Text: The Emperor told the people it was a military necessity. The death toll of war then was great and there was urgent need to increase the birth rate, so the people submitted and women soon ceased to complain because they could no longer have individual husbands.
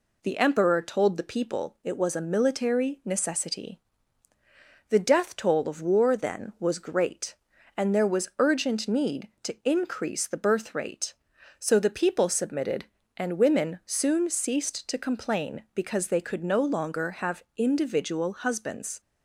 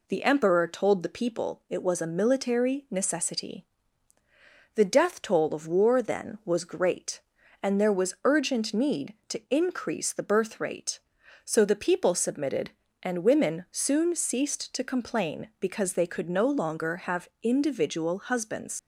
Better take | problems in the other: first | leaves "husbands" unfinished; at 18.7 s; 65 ms

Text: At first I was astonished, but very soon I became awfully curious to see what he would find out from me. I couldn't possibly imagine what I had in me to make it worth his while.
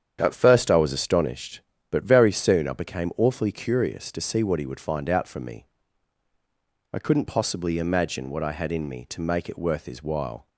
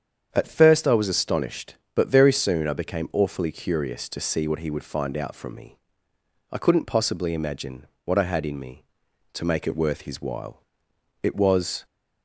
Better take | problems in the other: first | starts louder than the rest; strong; until 1.3 s; 8 dB; strong in the first // pauses between "imagine" and "what"; slight; at 7.8 s; 0.18 s long // goes on to say "It was"; noticeable; from 11.2 s on; 0.62 s long

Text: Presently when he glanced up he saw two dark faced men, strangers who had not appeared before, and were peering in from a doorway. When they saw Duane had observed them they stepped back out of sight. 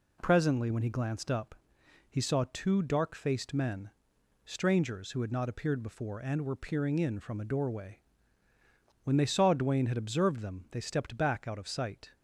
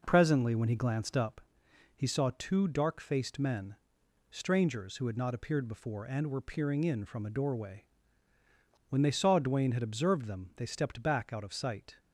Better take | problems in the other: first | starts louder than the rest; noticeable; until 1.3 s; 5 dB // pauses between "up" and "he"; noticeable; at 1.3 s; 0.56 s long; noticeable in the first

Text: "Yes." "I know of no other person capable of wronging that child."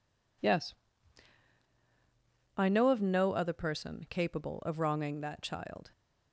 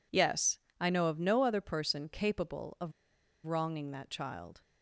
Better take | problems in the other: first | pauses between "of" and "wronging"; noticeable; at 2.9 s; 0.54 s long

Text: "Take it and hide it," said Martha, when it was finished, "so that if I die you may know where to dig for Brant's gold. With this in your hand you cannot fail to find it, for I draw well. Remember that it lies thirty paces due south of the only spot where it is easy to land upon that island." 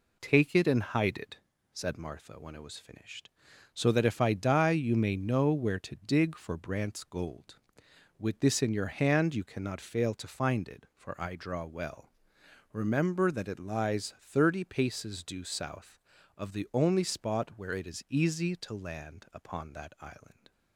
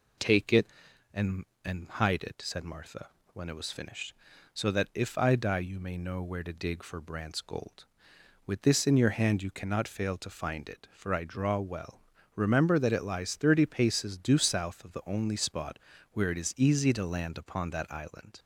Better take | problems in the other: first | says "and" twice; at 1.6 s // pauses between "spot" and "where"; slight; at 15.7 s; 0.34 s long

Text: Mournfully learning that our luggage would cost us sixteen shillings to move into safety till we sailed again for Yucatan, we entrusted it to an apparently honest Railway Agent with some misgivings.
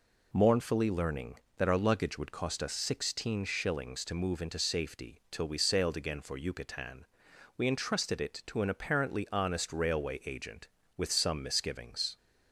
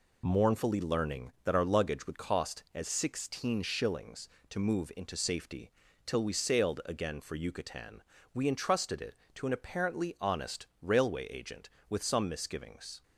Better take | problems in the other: first | says "as" for "us"; at 2.7 s // pauses between "safety" and "till"; slight; at 5.7 s; 0.36 s long // pauses between "honest" and "Railway"; slight; at 10.6 s; 0.16 s long

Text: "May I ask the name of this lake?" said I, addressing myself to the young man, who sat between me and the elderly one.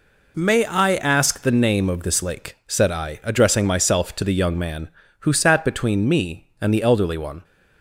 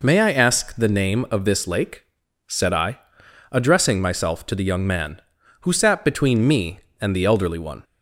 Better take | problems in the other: neither | none

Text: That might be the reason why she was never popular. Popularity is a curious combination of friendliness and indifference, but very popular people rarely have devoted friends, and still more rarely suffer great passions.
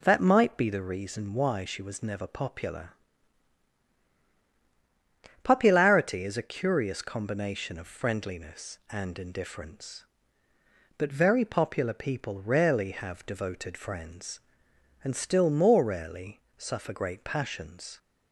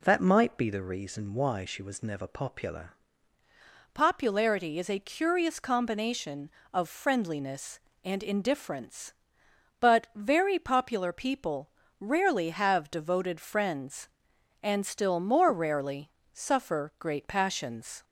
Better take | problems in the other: first | changes voice at "Popularity"; from 3.9 s on; 14.1 s long // pauses between "people" and "rarely"; slight; at 11.6 s; 0.28 s long // pauses between "rarely" and "suffer"; slight; at 16.0 s; 0.22 s long; slight in the first

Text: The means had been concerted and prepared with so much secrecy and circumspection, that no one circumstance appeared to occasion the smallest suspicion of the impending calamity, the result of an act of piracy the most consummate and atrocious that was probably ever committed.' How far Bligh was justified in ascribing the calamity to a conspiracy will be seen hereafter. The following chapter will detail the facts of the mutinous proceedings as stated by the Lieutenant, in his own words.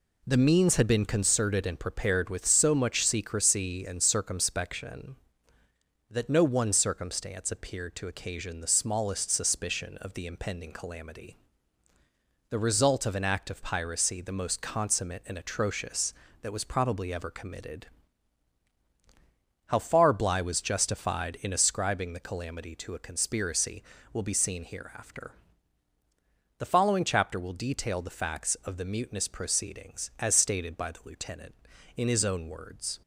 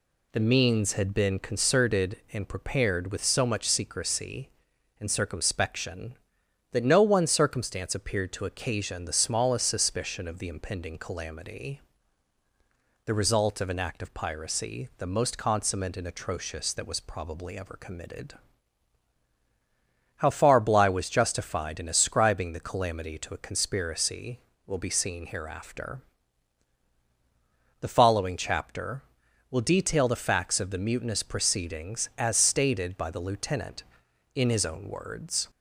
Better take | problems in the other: neither | none

